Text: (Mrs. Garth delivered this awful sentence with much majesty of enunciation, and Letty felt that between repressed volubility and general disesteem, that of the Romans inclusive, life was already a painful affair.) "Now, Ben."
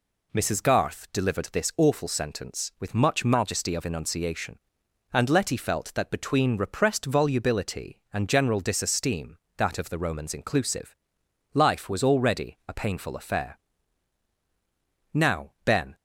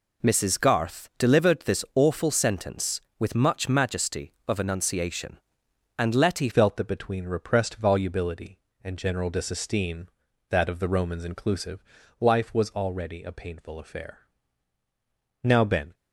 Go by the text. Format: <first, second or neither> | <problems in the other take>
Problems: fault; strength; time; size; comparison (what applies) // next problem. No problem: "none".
first | changes voice at "felt"; from 6.5 s on; 9.4 s long